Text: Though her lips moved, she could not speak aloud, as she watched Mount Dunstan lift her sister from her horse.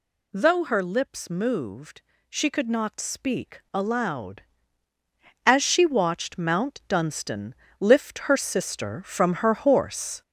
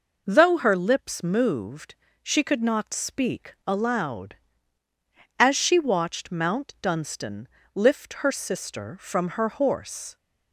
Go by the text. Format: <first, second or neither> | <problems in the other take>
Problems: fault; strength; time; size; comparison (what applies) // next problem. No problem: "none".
second | gets louder; noticeable; throughout; 6 dB // pauses between "Dunstan" and "lift"; slight; at 7.5 s; 0.26 s long; slight in the second